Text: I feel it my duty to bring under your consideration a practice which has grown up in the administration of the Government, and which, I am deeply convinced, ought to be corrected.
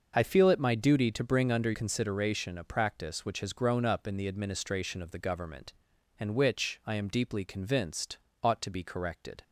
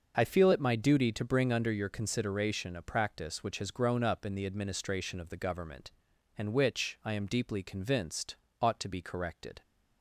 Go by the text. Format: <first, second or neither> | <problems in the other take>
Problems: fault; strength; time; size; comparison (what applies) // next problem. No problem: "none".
second | starts louder than the rest; noticeable; until 1.1 s; 6 dB // skips "your"; at 1.7 s